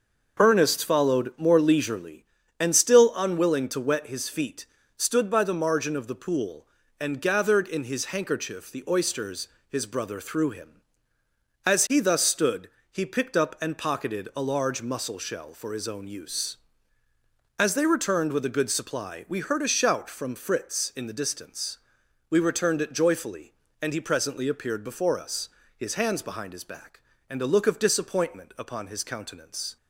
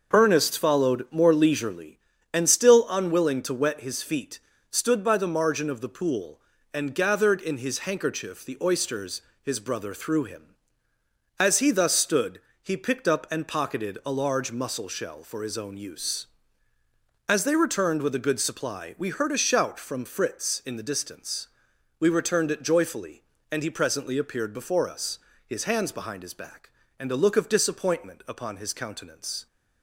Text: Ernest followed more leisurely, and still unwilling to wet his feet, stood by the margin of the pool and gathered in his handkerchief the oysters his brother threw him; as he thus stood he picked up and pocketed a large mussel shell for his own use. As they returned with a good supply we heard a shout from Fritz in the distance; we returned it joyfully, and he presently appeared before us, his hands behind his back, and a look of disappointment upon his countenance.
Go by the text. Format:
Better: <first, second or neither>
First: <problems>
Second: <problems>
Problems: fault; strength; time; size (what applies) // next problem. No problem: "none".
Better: neither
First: pauses between "oysters" and "his"; slight; at 9.4 s; 0.22 s long // pauses between "stood" and "he"; slight; at 12.6 s; 0.22 s long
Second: pauses between "oysters" and "his"; slight; at 9.1 s; 0.22 s long // pauses between "stood" and "he"; slight; at 12.3 s; 0.22 s long